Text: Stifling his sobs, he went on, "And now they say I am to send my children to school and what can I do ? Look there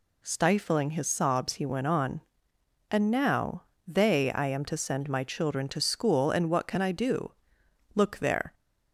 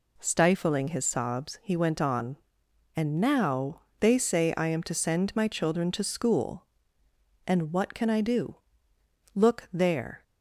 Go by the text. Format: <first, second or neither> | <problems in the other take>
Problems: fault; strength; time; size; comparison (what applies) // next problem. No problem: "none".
second | pauses between "now" and "they"; slight; at 3.6 s; 0.24 s long; slight in the second // skips "say"; at 4.3 s